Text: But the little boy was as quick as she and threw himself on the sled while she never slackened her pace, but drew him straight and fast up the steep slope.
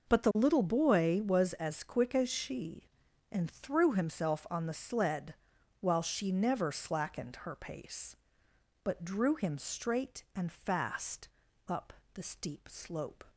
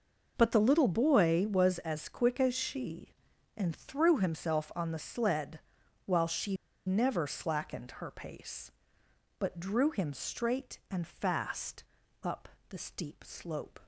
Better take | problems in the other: first | pauses between "sled" and "while"; at 5.5 s; 0.44 s long; also in the first // pauses between "she" and "never"; slight; at 6.5 s; 0.31 s long // pauses between "fast" and "up"; at 11.8 s; 0.40 s long; also in the first // pauses between "up" and "the"; slight; at 12.4 s; 0.22 s long; slight in the first

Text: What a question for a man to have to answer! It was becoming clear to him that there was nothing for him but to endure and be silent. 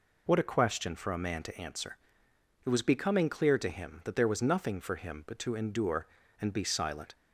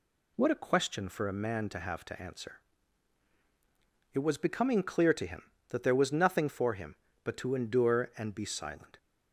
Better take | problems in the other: second | skips "to have"; at 1.4 s

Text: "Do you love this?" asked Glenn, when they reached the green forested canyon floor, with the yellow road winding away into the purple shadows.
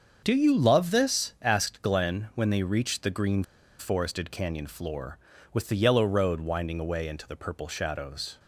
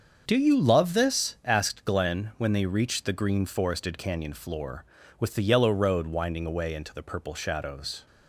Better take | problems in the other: second | starts louder than the rest; until 1.2 s; 7 dB; also in the second // pauses between "green" and "forested"; at 3.4 s; 0.36 s long

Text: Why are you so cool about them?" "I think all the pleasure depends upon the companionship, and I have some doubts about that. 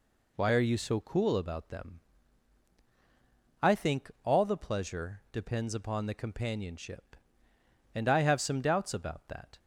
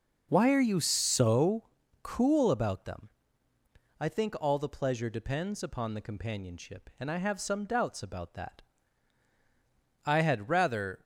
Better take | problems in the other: first | pauses between "so" and "cool"; at 1.6 s; 0.40 s long // goes on to say "I had rather"; noticeable; from 10.0 s on; 0.98 s long

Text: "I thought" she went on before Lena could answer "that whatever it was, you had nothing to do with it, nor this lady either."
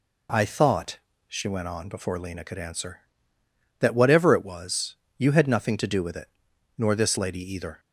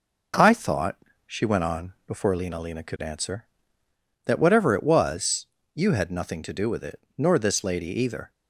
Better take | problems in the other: first | pauses between "thought" and "she"; slight; at 0.9 s; 0.26 s long; slight in the first // says "Lena" twice; at 2.5 s

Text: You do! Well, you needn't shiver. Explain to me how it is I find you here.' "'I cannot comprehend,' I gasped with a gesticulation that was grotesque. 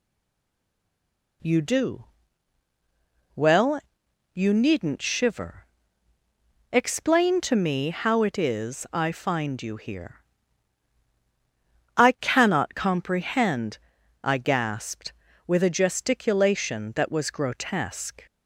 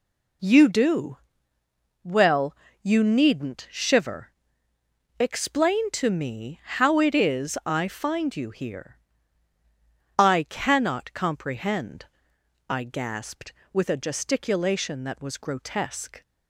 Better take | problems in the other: second | stays silent before the first word; noticeable; until 1.4 s; 1.4 s long

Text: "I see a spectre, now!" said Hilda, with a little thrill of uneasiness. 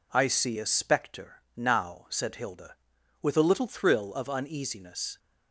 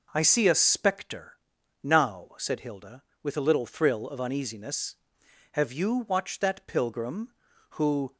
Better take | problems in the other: first | goes on to say "Have you watched that pilgrim who"; strong; from 5.5 s on; 2.6 s long

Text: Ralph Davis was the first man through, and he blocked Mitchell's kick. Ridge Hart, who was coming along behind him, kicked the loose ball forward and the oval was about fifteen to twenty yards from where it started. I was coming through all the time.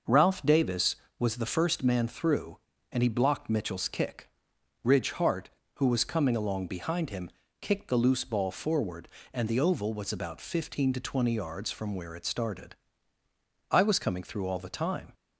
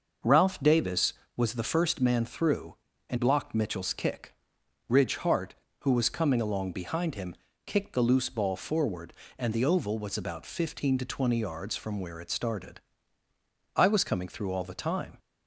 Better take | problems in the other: first | starts louder than the rest; noticeable; until 1.4 s; 6 dB; noticeable in the first // skips "he"; at 3.1 s

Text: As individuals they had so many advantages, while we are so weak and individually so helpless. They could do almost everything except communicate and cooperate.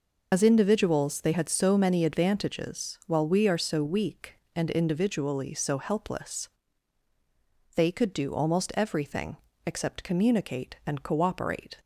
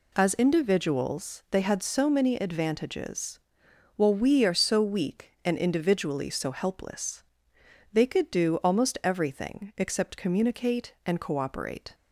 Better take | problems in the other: second | loses the start of "As"; at 0.3 s; 60 ms // pauses between "everything" and "except"; slight; at 9.3 s; 0.30 s long

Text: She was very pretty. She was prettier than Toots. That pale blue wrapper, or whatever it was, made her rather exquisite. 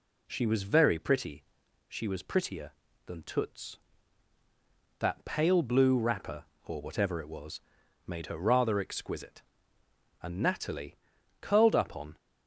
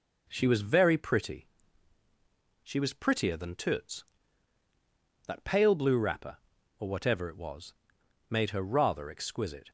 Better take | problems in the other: second | goes on to say "And Natalie curled up on"; strong; from 10.2 s on; 1.9 s long

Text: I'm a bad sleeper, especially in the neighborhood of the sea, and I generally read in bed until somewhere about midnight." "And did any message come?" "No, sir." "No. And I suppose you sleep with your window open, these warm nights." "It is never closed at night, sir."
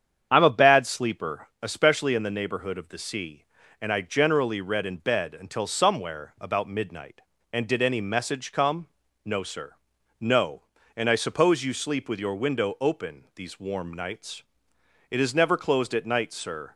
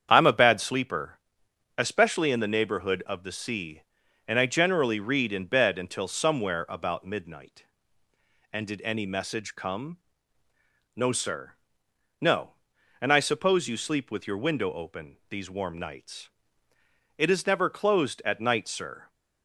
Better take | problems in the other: neither | starts louder than the rest; strong; the same in both

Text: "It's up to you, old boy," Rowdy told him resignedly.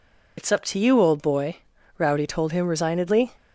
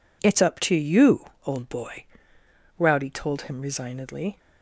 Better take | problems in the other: second | loses the start of "It's"; at 0.3 s; 65 ms

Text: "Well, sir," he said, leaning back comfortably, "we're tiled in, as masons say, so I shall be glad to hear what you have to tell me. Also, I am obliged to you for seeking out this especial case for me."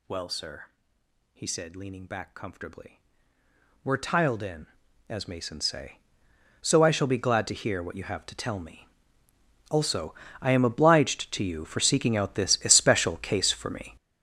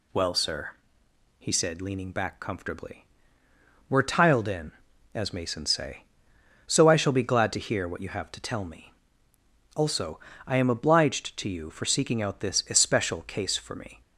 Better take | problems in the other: second | gets louder; strong; throughout; 12.5 dB

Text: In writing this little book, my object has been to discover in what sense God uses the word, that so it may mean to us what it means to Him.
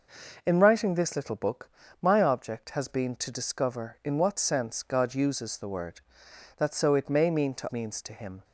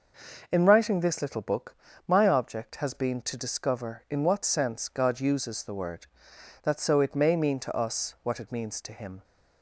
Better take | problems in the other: second | skips "us what it"; at 7.7 s

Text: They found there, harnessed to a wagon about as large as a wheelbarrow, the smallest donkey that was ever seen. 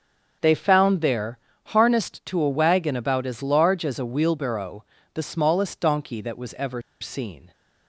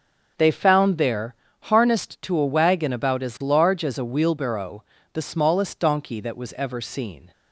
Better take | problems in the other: second | starts louder than the rest; strong; until 1.7 s; 7.5 dB; strong in the second // pauses between "ever" and "seen"; slight; at 6.8 s; 0.20 s long

